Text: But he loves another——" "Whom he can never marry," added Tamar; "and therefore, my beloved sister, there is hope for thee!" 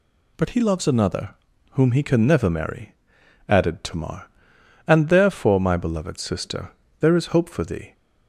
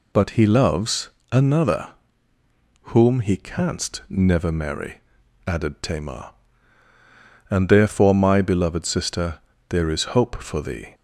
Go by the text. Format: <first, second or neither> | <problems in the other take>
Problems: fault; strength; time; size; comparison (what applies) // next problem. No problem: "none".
first | pauses between "loves" and "another"; slight; at 1.1 s; 0.20 s long // says "canst" for "can"; at 3.3 s